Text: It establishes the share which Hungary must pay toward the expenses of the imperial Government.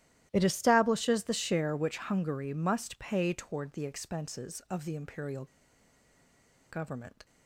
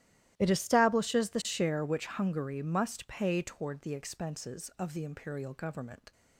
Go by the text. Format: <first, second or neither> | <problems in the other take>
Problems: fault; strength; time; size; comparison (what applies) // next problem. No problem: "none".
second | starts louder than the rest; strong; until 1.3 s; 14 dB; strong in the second // pauses between "imperial" and "Government"; strong; at 5.4 s; 1.2 s long